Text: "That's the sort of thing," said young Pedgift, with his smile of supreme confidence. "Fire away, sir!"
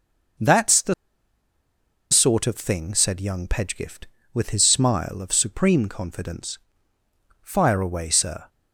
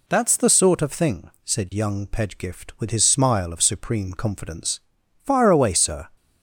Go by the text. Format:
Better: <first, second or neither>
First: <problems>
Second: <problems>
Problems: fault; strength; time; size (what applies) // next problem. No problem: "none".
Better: second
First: pauses between "the" and "sort"; at 0.9 s; 1.1 s long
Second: none